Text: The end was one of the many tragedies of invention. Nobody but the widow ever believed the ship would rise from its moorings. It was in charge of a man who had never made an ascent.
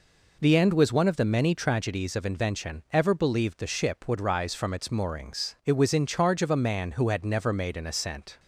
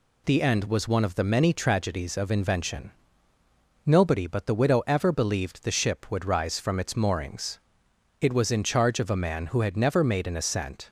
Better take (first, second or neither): second